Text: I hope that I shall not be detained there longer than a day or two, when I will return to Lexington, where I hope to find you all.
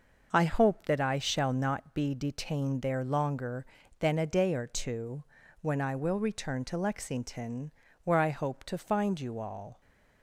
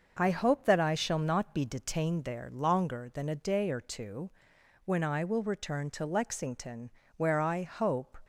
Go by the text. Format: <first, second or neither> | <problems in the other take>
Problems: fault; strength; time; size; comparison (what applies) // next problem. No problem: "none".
first | starts louder than the rest; until 1.2 s; 6.5 dB // stops before "to find you all"; at 8.2 s